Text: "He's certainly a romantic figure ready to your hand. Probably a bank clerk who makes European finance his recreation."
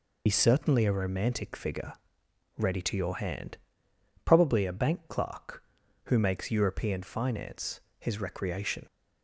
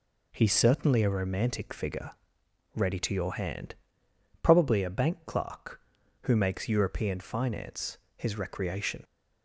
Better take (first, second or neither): second